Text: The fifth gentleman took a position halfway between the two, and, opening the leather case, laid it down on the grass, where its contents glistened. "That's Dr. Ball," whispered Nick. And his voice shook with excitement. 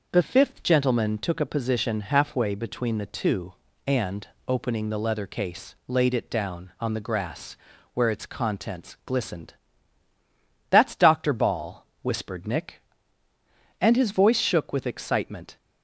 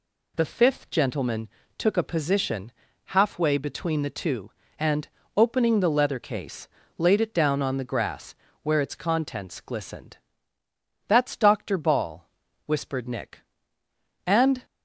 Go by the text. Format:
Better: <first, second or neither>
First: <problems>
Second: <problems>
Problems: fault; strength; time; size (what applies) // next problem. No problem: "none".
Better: first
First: none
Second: pauses between "gentleman" and "took"; slight; at 1.4 s; 0.28 s long // pauses between "position" and "halfway"; slight; at 2.7 s; 0.34 s long // stops before "his voice shook with excitement"; at 14.6 s